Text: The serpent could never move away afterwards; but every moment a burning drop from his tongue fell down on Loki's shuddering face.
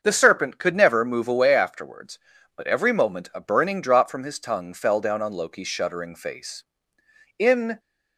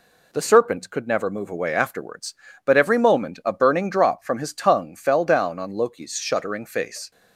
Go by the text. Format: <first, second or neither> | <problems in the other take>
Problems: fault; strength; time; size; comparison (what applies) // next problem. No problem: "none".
second | starts louder than the rest; until 1.0 s; 6.5 dB // goes on to say "In"; slight; from 7.3 s on; 0.40 s long